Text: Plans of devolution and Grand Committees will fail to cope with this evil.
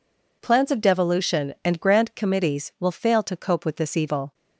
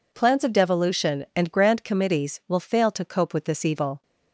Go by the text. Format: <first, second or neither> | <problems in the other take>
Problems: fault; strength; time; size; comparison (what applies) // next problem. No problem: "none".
neither | none